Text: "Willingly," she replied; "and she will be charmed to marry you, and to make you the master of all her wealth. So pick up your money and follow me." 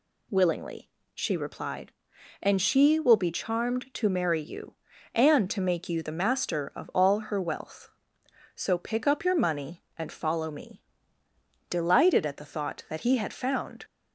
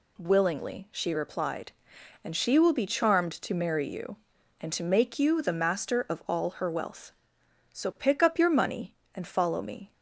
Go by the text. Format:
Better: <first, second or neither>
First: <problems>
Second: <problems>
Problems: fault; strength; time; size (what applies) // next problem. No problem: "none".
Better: second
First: goes on to say "Delighted at the thought that he had found"; strong; from 11.7 s on; 2.1 s long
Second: none